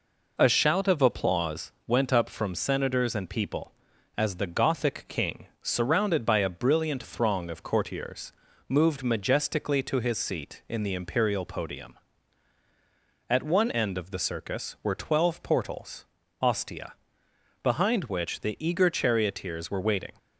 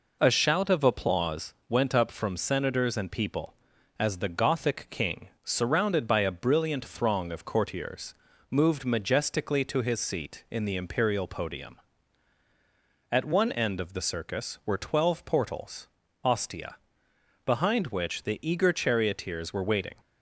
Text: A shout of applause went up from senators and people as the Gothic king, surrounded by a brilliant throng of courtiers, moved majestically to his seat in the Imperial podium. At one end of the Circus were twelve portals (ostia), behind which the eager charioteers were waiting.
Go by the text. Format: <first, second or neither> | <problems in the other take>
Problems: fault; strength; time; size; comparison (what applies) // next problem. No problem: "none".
neither | none